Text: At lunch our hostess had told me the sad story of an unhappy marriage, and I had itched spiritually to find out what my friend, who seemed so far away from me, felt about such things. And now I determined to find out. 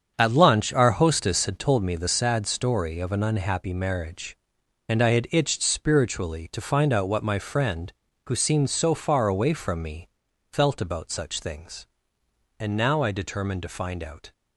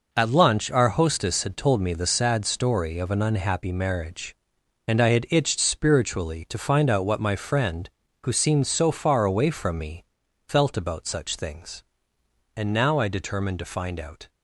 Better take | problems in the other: second | starts louder than the rest; strong; until 1.8 s; 7.5 dB

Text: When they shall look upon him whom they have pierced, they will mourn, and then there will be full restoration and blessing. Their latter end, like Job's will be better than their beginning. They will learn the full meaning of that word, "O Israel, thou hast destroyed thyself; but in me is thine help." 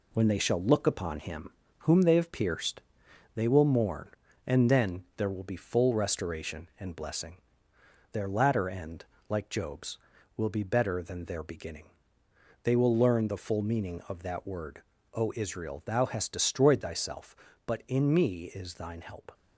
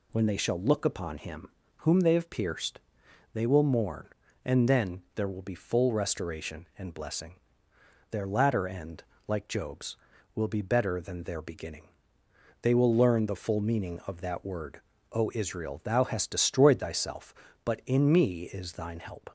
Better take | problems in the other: second | gets quieter; noticeable; throughout; 5 dB // pauses between "him" and "whom"; slight; at 1.5 s; 0.30 s long; slight in the second

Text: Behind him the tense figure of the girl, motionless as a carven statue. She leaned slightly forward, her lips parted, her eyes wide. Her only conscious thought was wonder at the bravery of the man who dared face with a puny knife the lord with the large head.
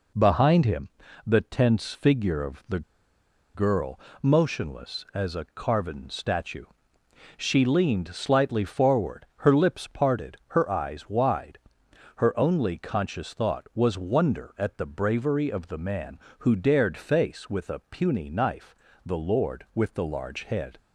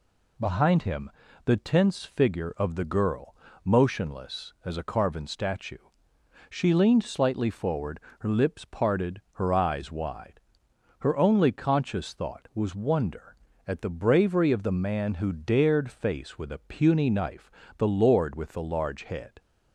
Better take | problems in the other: second | pauses between "him" and "the"; slight; at 0.8 s; 0.36 s long; slight in the second // pauses between "the" and "girl"; noticeable; at 2.8 s; 0.73 s long // pauses between "knife" and "the"; slight; at 18.7 s; 0.32 s long; slight in the second

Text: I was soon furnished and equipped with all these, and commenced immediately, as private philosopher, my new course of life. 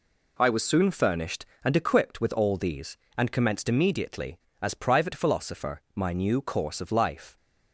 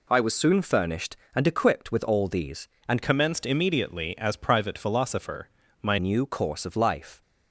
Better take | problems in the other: first | changes voice from "commenced" to "my"; from 3.0 to 5.9 s; 2.9 s long

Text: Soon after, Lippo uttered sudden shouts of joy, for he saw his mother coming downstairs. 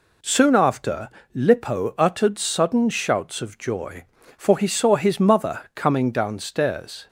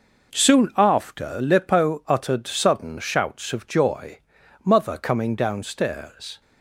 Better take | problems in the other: first | skips "for he saw his"; at 4.4 s

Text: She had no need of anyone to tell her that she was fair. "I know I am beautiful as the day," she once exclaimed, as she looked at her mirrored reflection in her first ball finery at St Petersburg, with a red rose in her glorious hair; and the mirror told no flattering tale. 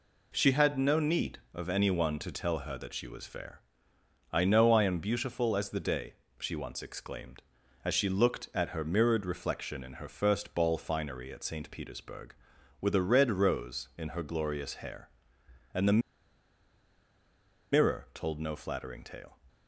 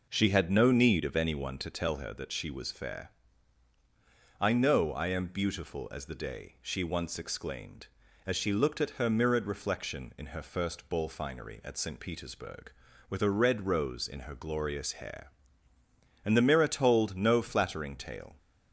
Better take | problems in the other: second | pauses between "the" and "mirror"; strong; at 16.0 s; 1.7 s long

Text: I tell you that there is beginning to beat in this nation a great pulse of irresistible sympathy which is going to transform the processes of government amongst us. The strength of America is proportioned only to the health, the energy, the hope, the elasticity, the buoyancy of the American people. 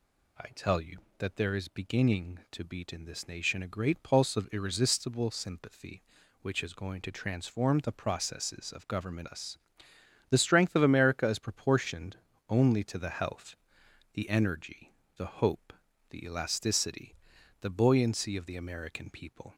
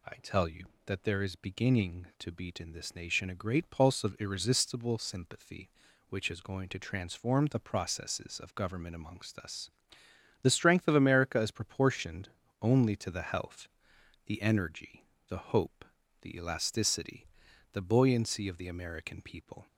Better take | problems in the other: second | skips "amongst"; at 9.2 s // pauses between "proportioned" and "only"; slight; at 12.1 s; 0.32 s long; slight in the second

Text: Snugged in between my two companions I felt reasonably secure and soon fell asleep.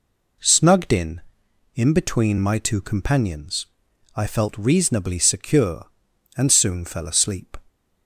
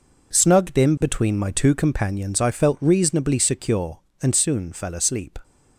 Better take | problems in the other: second | says "in" twice; at 1.7 s // pauses between "companions" and "I"; noticeable; at 3.6 s; 0.48 s long

